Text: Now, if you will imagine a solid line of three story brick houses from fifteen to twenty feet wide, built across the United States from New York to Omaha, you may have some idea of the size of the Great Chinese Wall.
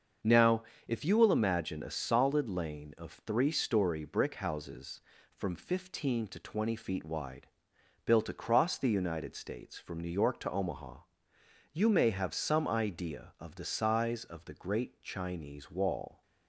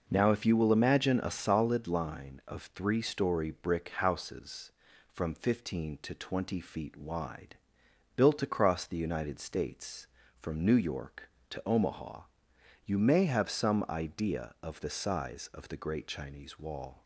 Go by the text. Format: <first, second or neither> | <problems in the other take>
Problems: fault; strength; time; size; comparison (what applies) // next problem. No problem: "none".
second | starts louder than the rest; until 1.4 s; 6.5 dB // says "lane" for "line"; at 2.4 s